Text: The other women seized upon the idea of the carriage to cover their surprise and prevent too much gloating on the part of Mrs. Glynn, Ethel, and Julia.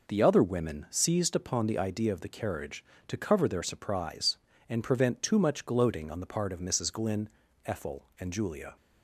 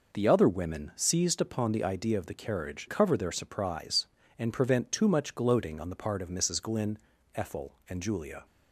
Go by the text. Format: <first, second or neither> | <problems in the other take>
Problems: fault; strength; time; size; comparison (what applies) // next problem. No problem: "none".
first | skips "to"; at 2.8 s